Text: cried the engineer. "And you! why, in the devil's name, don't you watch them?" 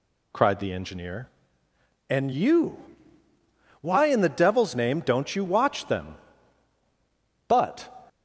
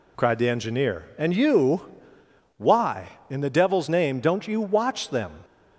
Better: second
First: goes on to say "But"; slight; from 7.4 s on; 0.42 s long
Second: none

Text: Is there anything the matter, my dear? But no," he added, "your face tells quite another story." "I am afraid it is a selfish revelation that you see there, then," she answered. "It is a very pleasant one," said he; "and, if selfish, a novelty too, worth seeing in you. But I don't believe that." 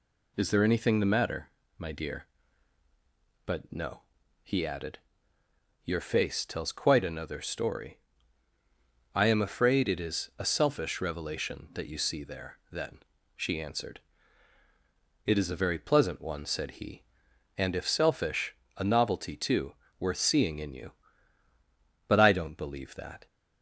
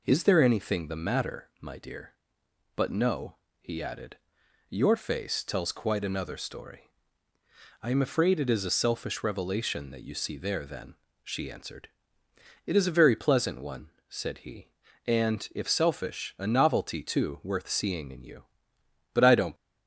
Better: first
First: none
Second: stops before "believe that"; at 19.5 s

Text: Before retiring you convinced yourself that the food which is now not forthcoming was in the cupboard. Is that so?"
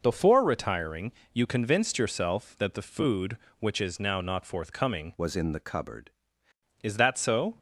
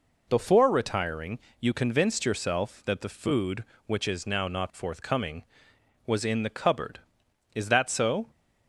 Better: second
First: pauses between "retiring" and "you"; slight; at 1.1 s; 0.22 s long // changes voice from "was" to "cupboard"; from 5.1 to 6.1 s; 1.0 s long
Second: pauses between "retiring" and "you"; slight; at 1.3 s; 0.22 s long

